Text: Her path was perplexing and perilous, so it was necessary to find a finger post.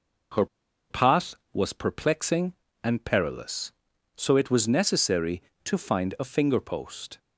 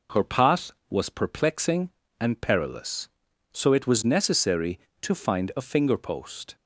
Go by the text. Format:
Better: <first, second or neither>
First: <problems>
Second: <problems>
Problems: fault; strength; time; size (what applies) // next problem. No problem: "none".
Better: second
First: pauses between "Her" and "path"; at 0.4 s; 0.43 s long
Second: none